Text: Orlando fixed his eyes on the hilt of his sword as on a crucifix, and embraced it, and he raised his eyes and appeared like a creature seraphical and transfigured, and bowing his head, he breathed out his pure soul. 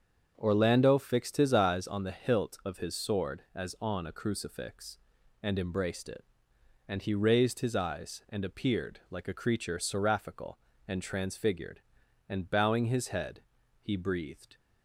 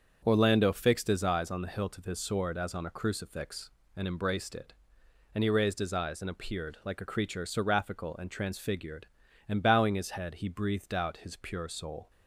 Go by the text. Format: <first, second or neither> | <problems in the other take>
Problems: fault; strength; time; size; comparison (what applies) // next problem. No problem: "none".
second | starts louder than the rest; until 1.3 s; 7 dB; also in the second // stops before "out his pure soul"; at 14.5 s